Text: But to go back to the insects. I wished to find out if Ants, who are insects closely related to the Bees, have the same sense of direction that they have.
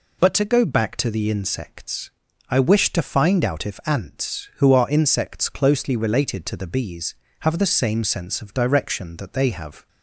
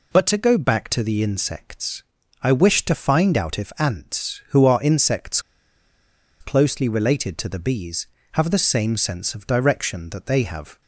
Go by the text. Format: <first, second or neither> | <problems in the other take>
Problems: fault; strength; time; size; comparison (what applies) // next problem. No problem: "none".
first | pauses between "insects" and "closely"; at 5.4 s; 1.0 s long